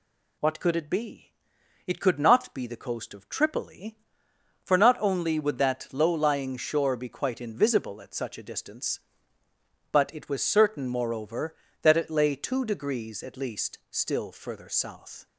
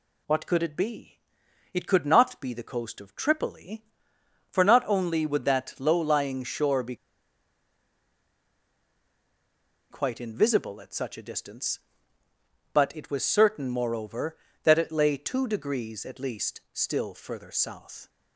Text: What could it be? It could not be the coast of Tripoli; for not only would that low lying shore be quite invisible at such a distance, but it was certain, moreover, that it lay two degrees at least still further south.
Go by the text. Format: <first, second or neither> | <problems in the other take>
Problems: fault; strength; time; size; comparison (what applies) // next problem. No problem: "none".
first | pauses between "be" and "quite"; strong; at 6.9 s; 2.9 s long